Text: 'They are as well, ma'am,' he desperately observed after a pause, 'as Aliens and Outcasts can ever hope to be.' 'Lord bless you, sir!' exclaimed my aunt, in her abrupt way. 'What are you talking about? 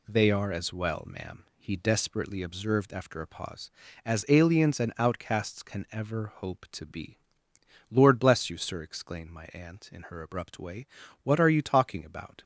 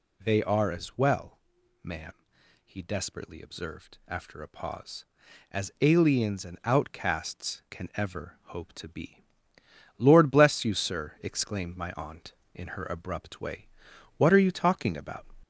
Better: first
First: none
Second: gets louder; slight; throughout; 2.5 dB

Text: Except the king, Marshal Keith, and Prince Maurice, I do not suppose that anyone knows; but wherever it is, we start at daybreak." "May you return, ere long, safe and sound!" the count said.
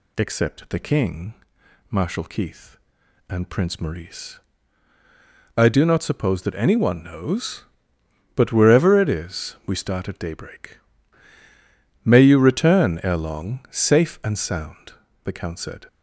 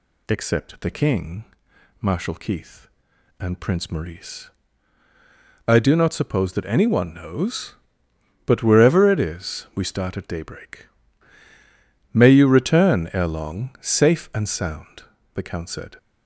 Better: neither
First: none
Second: none

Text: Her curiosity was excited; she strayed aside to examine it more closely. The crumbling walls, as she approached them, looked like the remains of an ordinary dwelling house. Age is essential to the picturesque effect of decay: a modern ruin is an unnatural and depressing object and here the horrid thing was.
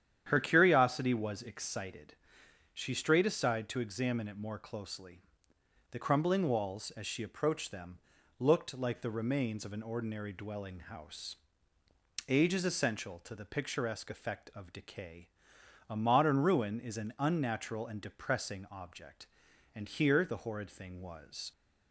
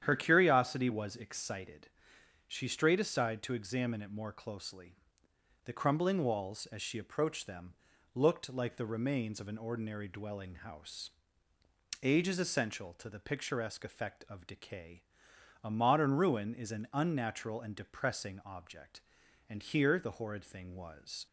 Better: neither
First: starts louder than the rest; strong; until 1.2 s; 9.5 dB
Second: starts louder than the rest; strong; until 1.0 s; 9.5 dB

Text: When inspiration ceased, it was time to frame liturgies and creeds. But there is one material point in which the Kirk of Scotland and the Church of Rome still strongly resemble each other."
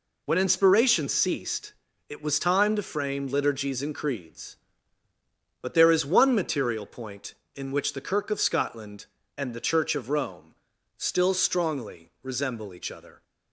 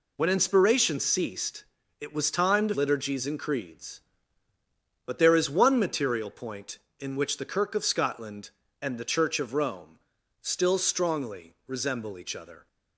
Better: first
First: pauses between "Rome" and "still"; at 10.5 s; 0.42 s long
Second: skips "frame"; at 2.7 s // pauses between "Rome" and "still"; at 9.9 s; 0.42 s long

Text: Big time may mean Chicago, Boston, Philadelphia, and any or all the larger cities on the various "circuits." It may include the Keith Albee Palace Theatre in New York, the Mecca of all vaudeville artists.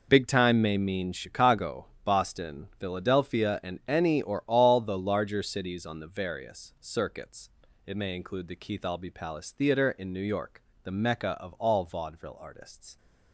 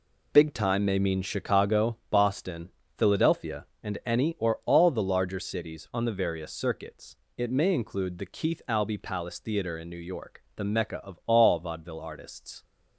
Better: neither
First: none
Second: none

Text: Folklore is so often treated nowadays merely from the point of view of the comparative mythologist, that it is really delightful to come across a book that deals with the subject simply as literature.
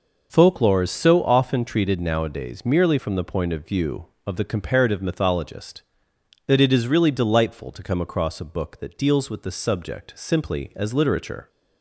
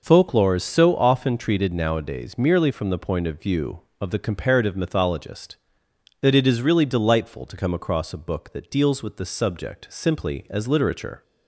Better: neither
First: none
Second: none

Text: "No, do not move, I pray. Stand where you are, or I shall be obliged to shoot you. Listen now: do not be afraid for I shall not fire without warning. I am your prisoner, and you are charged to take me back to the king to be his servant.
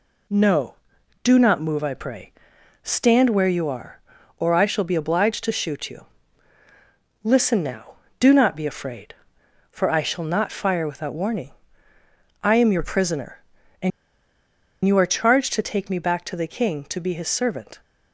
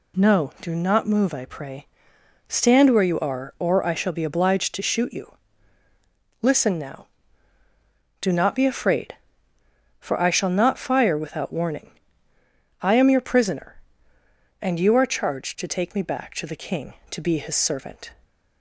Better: second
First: pauses between "and" and "you"; noticeable; at 13.9 s; 0.95 s long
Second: none

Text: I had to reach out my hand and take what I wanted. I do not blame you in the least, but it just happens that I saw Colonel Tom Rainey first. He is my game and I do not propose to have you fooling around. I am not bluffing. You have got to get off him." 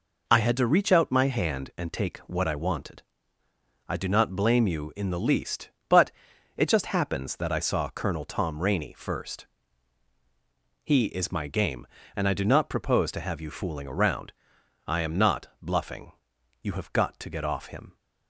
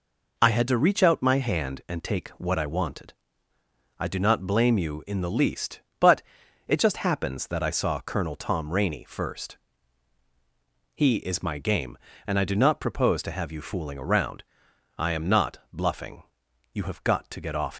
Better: first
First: pauses between "but" and "it"; noticeable; at 6.0 s; 0.46 s long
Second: pauses between "but" and "it"; noticeable; at 6.2 s; 0.46 s long // stops before "him"; at 17.7 s

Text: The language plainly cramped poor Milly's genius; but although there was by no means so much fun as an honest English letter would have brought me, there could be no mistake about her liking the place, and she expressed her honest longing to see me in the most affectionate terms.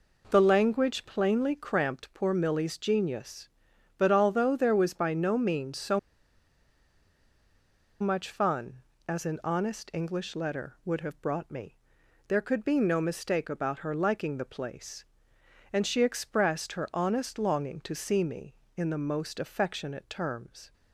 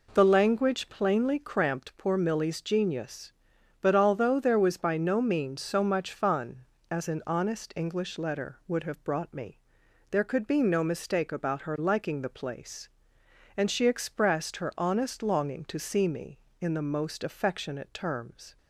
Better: second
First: pauses between "so" and "much"; strong; at 5.9 s; 2.0 s long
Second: none

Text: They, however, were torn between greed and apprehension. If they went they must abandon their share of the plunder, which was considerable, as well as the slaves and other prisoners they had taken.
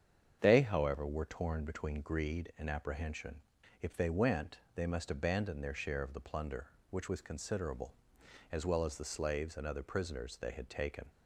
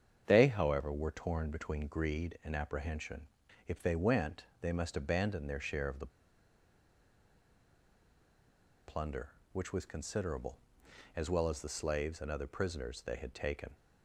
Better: first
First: starts louder than the rest; strong; until 1.4 s; 8 dB // pauses between "went" and "they"; slight; at 4.5 s; 0.18 s long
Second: starts louder than the rest; strong; until 1.2 s; 8 dB // pauses between "went" and "they"; slight; at 4.4 s; 0.18 s long // pauses between "the" and "plunder"; strong; at 6.1 s; 2.7 s long

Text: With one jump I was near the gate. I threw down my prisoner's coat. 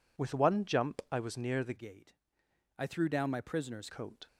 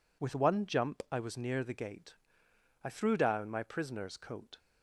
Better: second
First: changes voice from "gate" to "prisoner's"; from 1.7 to 3.8 s; 2.1 s long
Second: none

